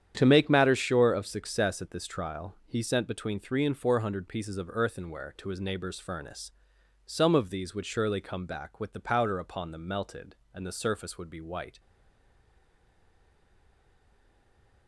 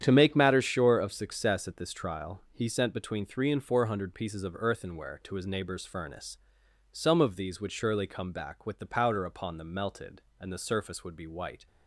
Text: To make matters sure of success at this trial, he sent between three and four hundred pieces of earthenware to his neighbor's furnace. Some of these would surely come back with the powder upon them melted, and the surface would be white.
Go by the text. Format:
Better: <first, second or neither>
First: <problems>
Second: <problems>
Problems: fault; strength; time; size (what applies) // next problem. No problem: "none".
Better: second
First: starts louder than the rest; strong; until 1.1 s; 9.5 dB // stays silent after the last word; strong; from 11.7 s on; 3.1 s long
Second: starts louder than the rest; strong; until 1.0 s; 9.5 dB